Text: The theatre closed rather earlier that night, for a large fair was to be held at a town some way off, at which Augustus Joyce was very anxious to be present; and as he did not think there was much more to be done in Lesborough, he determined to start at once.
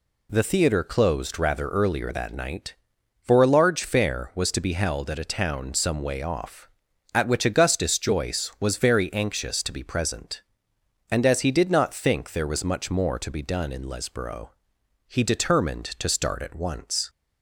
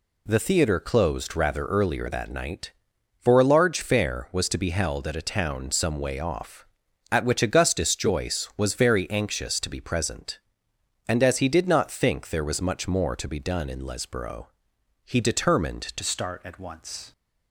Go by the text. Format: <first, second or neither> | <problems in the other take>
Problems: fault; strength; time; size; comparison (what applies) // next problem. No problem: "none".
first | changes voice at "start"; from 16.0 s on; 1.1 s long